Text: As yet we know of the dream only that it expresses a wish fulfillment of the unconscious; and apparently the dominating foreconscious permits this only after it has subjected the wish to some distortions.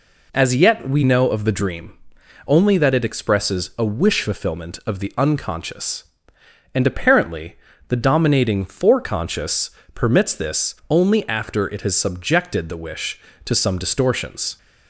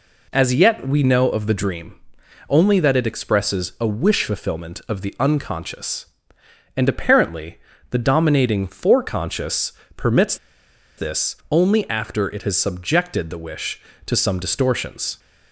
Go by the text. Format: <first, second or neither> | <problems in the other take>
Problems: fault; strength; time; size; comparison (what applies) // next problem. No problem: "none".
first | pauses between "dream" and "only"; noticeable; at 1.9 s; 0.56 s long; noticeable in the first // pauses between "apparently" and "the"; slight; at 7.5 s; 0.32 s long; slight in the first // pauses between "foreconscious" and "permits"; slight; at 9.7 s; 0.24 s long; slight in the first // pauses between "permits" and "this"; noticeable; at 10.3 s; 0.62 s long